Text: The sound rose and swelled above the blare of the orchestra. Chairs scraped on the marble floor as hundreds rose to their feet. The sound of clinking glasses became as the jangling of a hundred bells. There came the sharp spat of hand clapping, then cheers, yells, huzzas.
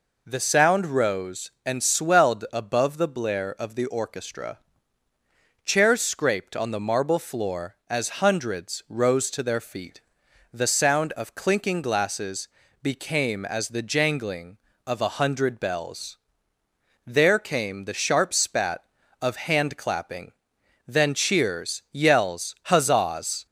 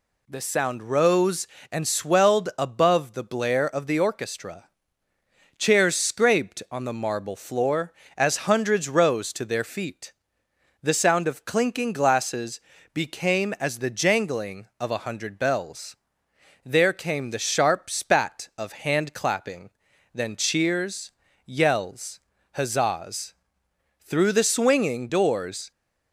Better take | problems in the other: first | pauses between "glasses" and "became"; slight; at 12.5 s; 0.34 s long; slight in the first // goes on to say "Through the swinging doors"; strong; from 24.0 s on; 1.6 s long

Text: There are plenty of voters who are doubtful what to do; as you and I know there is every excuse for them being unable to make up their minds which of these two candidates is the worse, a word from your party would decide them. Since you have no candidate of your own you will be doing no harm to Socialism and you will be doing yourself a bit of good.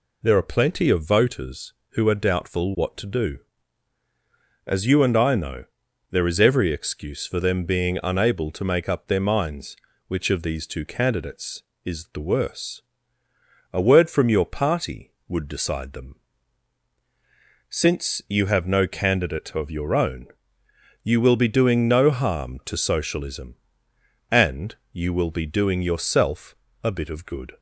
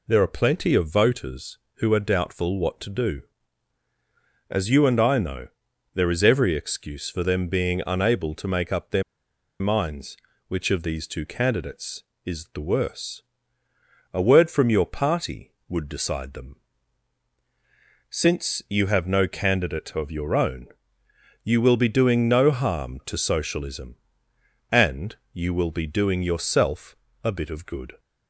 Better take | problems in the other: first | pauses between "know" and "there"; noticeable; at 5.4 s; 0.46 s long; noticeable in the first // pauses between "their" and "minds"; noticeable; at 9.0 s; 0.58 s long // pauses between "own" and "you"; noticeable; at 20.6 s; 0.78 s long; noticeable in the first // pauses between "and" and "you"; slight; at 25.1 s; 0.18 s long; slight in the first // pauses between "yourself" and "a"; slight; at 26.9 s; 0.26 s long; slight in the first

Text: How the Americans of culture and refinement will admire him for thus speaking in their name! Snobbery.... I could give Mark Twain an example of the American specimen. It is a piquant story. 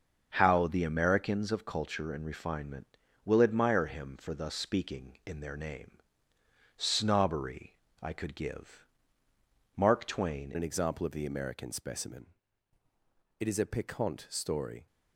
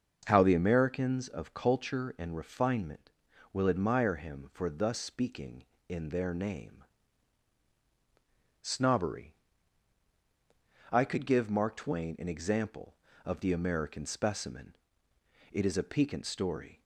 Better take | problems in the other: second | starts louder than the rest; until 1.3 s; 6.5 dB; also in the second // pauses between "give" and "Mark"; noticeable; at 8.8 s; 0.90 s long // changes voice at "an"; from 10.5 s on; 4.3 s long

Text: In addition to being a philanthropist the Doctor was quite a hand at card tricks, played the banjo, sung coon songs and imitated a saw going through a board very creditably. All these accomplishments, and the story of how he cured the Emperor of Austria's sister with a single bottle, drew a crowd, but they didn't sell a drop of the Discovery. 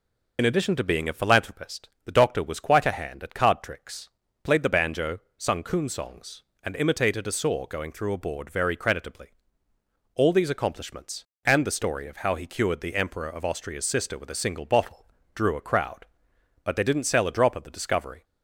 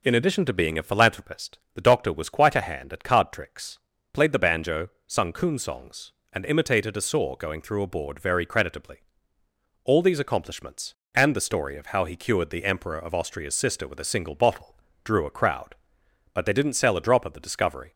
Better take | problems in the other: second | loses the start of "In"; at 0.3 s; 35 ms // pauses between "philanthropist" and "the"; slight; at 1.8 s; 0.16 s long; slight in the second

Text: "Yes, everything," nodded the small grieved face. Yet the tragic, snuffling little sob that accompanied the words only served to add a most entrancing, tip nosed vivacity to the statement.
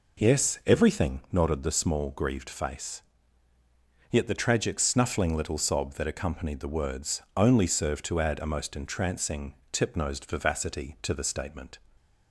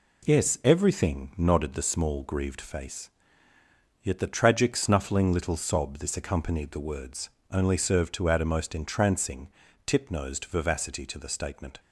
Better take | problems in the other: first | says "this" for "that"; at 5.9 s // pauses between "words" and "only"; slight; at 7.2 s; 0.24 s long

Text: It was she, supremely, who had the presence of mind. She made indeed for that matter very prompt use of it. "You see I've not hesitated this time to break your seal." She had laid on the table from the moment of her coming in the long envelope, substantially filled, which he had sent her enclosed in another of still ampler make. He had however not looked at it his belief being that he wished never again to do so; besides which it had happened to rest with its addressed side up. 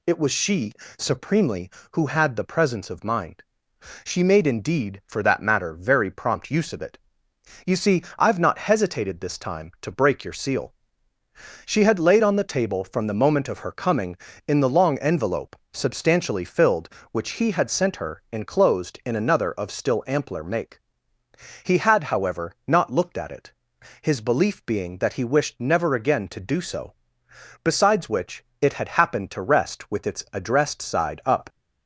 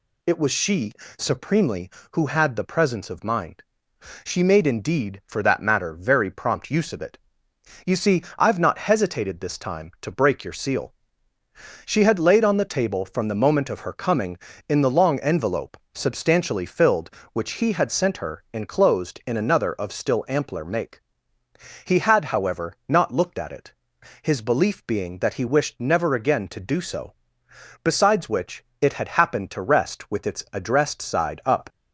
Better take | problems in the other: neither | pauses between "see" and "I've"; slight; the same in both // pauses between "it" and "his"; noticeable; the same in both // pauses between "which" and "it"; slight; the same in both

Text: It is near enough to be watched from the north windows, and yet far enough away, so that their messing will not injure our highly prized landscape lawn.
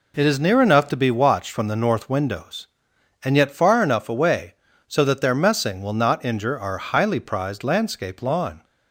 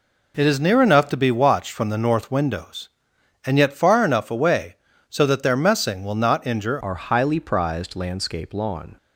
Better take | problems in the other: first | changes voice at "our"; from 6.8 s on; 2.1 s long

